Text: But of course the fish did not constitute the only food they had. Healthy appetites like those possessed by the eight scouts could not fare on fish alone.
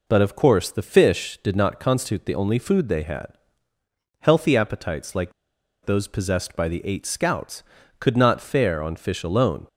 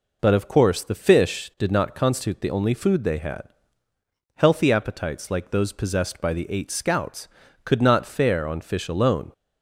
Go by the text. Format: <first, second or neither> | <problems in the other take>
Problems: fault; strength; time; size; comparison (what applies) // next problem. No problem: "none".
second | pauses between "like" and "those"; noticeable; at 5.3 s; 0.53 s long